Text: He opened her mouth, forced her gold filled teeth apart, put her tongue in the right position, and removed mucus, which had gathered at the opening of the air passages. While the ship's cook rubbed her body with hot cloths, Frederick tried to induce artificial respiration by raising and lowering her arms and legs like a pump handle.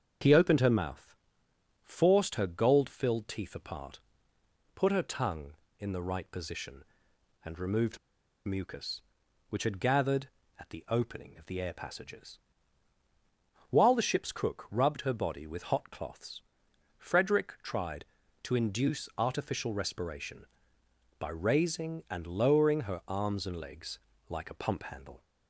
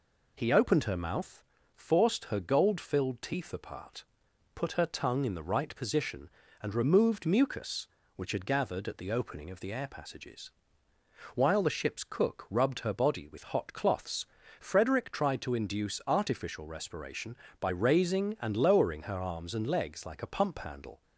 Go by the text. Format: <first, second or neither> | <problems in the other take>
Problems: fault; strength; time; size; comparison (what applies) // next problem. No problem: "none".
second | starts louder than the rest; until 1.8 s; 7 dB // pauses between "removed" and "mucus"; noticeable; at 7.9 s; 0.47 s long // pauses between "legs" and "like"; slight; at 23.9 s; 0.32 s long